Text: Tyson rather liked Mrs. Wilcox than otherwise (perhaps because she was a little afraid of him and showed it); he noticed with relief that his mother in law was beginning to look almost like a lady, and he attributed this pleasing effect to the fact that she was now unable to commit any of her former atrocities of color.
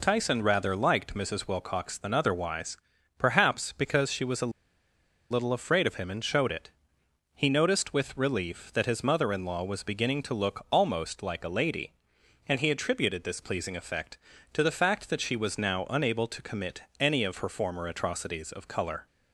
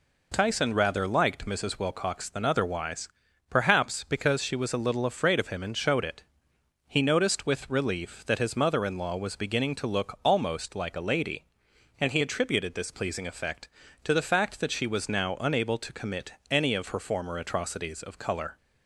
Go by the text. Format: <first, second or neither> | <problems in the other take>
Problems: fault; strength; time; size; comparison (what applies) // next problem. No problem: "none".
second | pauses between "a" and "little"; noticeable; at 4.4 s; 0.81 s long